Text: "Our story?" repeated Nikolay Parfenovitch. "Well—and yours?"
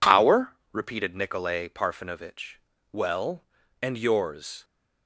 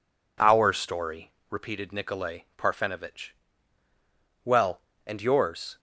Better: second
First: skips "story"; at 0.6 s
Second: none

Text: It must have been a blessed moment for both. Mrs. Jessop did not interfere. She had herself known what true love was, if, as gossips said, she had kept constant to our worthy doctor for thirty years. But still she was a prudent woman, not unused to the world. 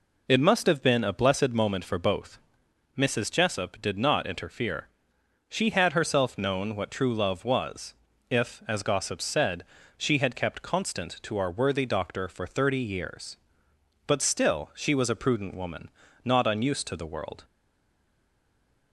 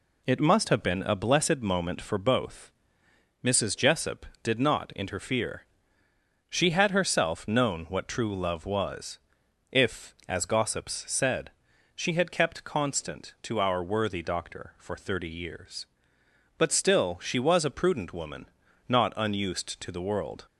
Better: second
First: stays silent after the last word; noticeable; from 17.4 s on; 1.5 s long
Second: none

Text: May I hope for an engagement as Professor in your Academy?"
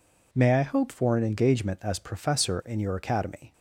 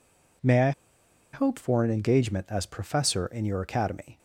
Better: first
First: none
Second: pauses between "I" and "hope"; noticeable; at 0.7 s; 0.62 s long

